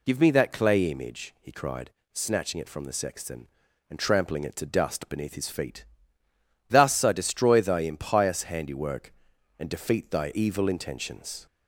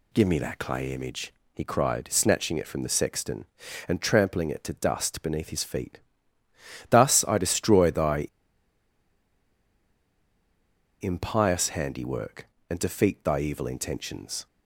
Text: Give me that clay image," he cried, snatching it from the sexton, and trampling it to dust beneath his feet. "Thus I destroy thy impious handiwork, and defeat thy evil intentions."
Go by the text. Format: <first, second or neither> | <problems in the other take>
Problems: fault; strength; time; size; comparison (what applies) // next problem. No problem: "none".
first | pauses between "thy" and "impious"; strong; at 8.2 s; 2.7 s long